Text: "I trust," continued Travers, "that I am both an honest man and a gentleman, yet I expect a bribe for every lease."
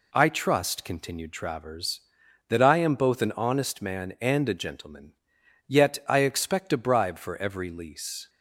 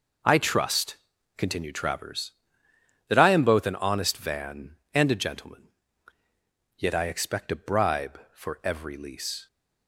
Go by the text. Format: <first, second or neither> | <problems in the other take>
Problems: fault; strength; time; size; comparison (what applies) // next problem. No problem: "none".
first | says "van" for "man"; at 4.1 s